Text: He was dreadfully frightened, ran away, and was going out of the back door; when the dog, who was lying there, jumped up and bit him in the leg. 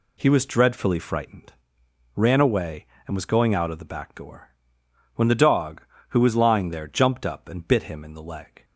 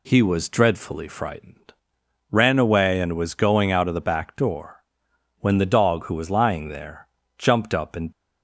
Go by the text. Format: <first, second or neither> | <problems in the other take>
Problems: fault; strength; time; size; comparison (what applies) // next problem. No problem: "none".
first | stops before "bit him in the leg"; at 8.1 s